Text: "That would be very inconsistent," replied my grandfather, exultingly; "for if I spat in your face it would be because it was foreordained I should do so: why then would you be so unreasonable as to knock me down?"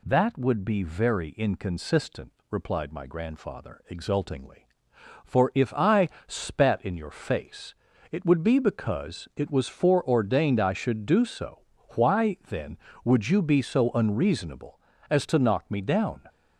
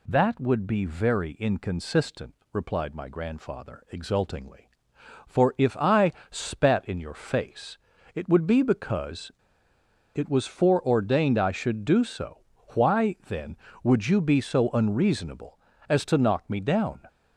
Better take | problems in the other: first | pauses between "I" and "spat"; slight; at 6.1 s; 0.18 s long; slight in the first // pauses between "face" and "it"; at 7.7 s; 0.38 s long; also in the first // pauses between "because" and "it"; noticeable; at 9.3 s; 0.83 s long

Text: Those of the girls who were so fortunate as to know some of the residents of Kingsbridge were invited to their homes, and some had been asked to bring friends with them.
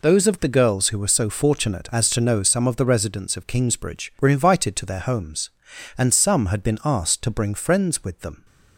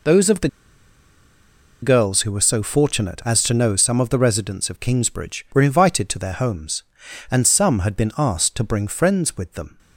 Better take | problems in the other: first | pauses between "the" and "girls"; strong; at 0.4 s; 1.3 s long

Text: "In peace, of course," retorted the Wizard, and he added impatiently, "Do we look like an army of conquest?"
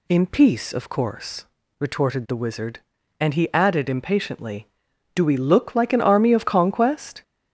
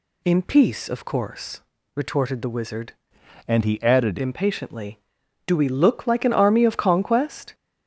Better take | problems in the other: first | changes voice from "and" to "added"; from 3.4 to 4.1 s; 0.7 s long

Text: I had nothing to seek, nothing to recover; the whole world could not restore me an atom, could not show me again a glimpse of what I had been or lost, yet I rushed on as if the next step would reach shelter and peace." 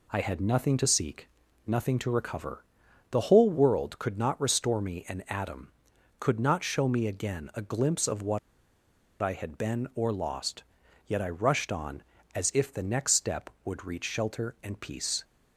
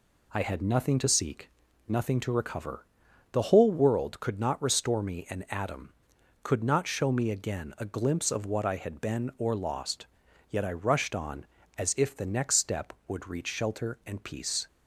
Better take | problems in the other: second | pauses between "what" and "I"; noticeable; at 8.3 s; 0.82 s long

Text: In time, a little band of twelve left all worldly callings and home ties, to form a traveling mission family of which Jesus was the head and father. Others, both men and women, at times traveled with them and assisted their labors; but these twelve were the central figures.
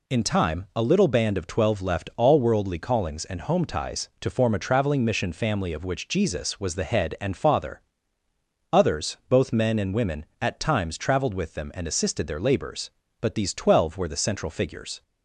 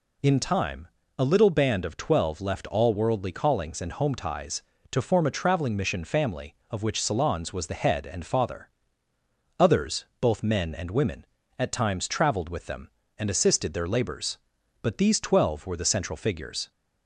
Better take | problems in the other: first | says "Salons" for "Jesus"; at 7.0 s

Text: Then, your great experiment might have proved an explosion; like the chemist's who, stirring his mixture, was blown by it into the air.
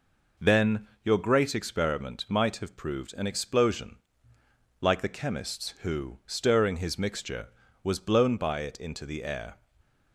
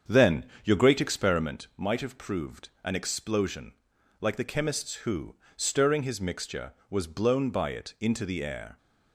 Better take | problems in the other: first | starts louder than the rest; strong; until 1.7 s; 7.5 dB // pauses between "proved" and "an"; slight; at 2.6 s; 0.16 s long

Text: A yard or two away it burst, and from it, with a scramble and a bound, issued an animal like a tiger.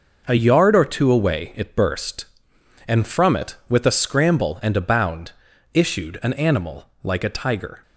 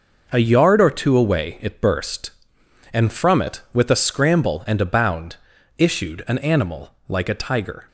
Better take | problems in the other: neither | pauses between "animal" and "like"; slight; the same in both

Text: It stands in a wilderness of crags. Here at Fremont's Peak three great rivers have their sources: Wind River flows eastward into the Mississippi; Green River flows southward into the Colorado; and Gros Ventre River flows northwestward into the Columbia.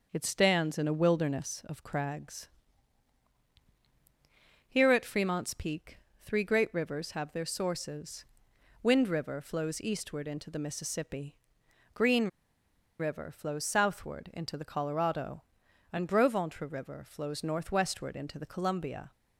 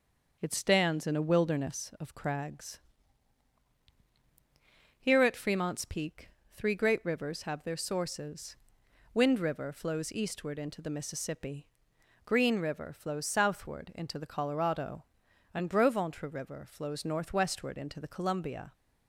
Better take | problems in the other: second | starts louder than the rest; until 1.1 s; 6.5 dB; also in the second // pauses between "Peak" and "three"; slight; at 5.9 s; 0.26 s long; slight in the second // pauses between "Green" and "River"; noticeable; at 12.2 s; 0.72 s long

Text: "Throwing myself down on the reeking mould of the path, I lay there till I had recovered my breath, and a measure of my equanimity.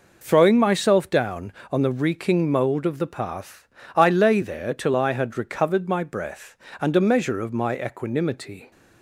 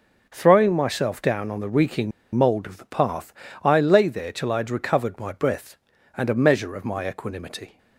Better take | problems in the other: first | pauses between "reeking" and "mould"; slight; at 2.1 s; 0.24 s long

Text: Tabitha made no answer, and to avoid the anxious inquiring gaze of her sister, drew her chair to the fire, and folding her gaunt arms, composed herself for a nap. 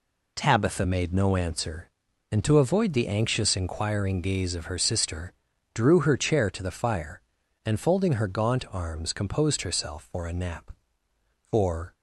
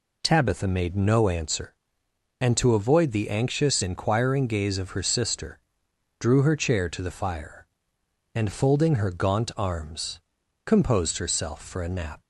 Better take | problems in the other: second | goes on to say "For"; slight; from 11.4 s on; 0.44 s long

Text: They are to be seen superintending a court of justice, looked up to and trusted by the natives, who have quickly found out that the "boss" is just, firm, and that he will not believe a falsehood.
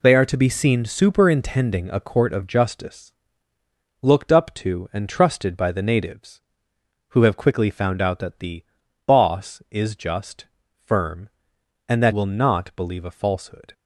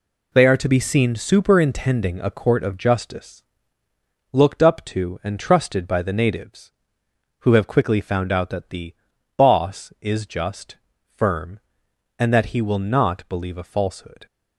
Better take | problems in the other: second | pauses between "the" and "boss"; at 8.6 s; 0.42 s long; also in the second // skips "he"; at 12.1 s

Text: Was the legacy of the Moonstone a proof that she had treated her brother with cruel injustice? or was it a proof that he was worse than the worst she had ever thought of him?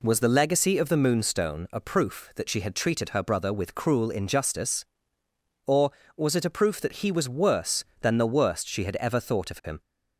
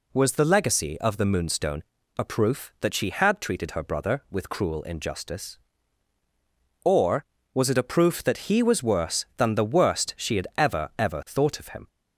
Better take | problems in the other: first | pauses between "Moonstone" and "a"; slight; at 1.8 s; 0.34 s long // says "ever" twice; at 10.9 s

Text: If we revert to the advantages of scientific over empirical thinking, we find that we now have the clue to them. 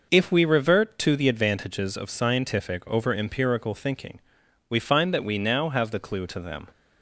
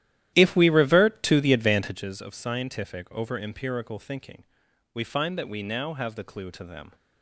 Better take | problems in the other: first | starts louder than the rest; strong; until 2.0 s; 13 dB

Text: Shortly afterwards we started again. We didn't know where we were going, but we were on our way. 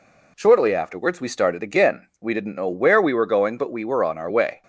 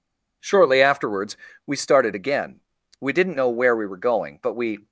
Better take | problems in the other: first | pauses between "afterwards" and "we"; slight; at 1.3 s; 0.30 s long // stops before "were on our way"; at 4.8 s

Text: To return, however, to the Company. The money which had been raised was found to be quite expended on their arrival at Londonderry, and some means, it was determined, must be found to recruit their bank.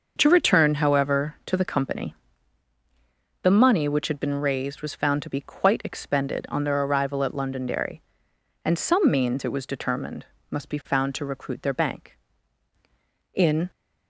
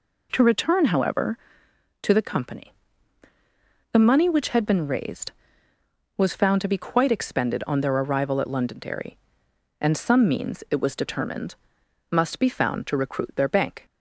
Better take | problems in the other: second | starts louder than the rest; until 1.1 s; 6.5 dB // goes on to say "In"; slight; from 13.3 s on; 0.38 s long

